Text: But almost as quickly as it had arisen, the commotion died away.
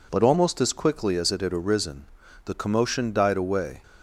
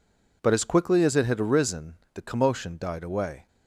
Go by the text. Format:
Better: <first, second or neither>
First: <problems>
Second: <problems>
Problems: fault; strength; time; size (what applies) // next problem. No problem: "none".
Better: first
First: none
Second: skips "almost"; at 0.5 s